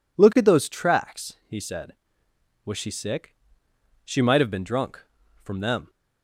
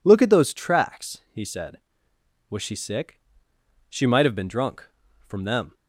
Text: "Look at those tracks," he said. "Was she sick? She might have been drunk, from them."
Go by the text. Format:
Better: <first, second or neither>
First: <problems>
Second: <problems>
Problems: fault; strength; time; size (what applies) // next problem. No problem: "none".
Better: neither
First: none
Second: none